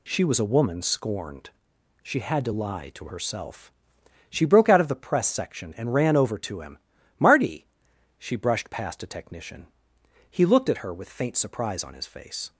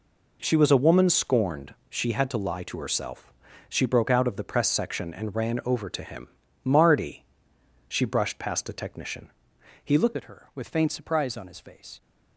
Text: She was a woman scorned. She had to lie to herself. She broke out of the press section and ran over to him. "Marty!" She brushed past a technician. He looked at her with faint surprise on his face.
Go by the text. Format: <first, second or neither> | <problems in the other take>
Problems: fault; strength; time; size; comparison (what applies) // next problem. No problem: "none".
first | changes voice at "at"; from 10.1 s on; 1.9 s long